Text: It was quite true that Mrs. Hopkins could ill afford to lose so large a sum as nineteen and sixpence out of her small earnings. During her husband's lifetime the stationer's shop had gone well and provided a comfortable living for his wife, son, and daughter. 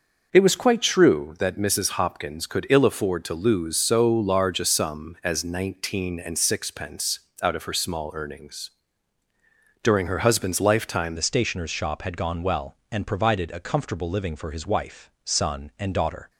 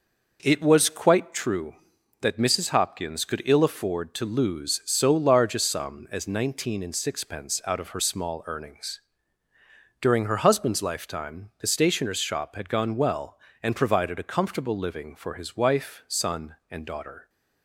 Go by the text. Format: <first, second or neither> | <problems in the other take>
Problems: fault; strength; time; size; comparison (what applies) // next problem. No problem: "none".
second | pauses between "sixpence" and "out"; slight; at 7.1 s; 0.22 s long // changes voice at "the"; from 11.1 s on; 5.1 s long